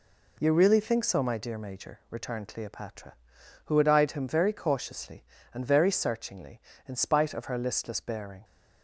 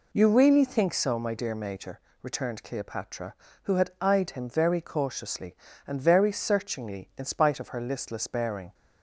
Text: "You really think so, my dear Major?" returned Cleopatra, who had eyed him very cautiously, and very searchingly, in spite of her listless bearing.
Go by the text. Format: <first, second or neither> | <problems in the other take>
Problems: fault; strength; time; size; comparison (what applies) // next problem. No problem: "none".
neither | none